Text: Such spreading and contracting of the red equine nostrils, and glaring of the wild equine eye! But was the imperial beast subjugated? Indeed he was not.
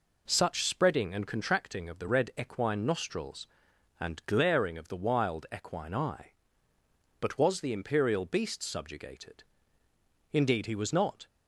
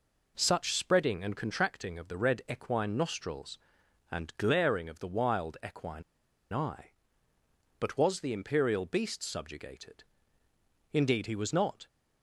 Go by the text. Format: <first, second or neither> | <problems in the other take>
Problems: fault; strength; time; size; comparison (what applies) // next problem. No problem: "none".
first | pauses between "equine" and "eye"; noticeable; at 6.0 s; 0.50 s long